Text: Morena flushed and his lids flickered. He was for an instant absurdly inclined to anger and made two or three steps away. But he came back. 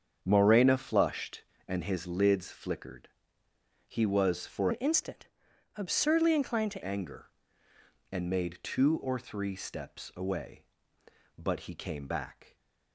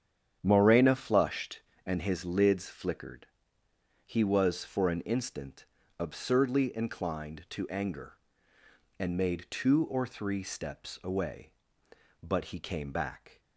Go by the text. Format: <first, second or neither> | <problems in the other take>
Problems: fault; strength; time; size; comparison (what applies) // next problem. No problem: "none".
second | starts louder than the rest; strong; until 1.2 s; 8 dB; strong in the second // changes voice from "an" to "to"; from 4.7 to 6.8 s; 2.1 s long // pauses between "instant" and "absurdly"; noticeable; at 5.2 s; 0.48 s long; slight in the second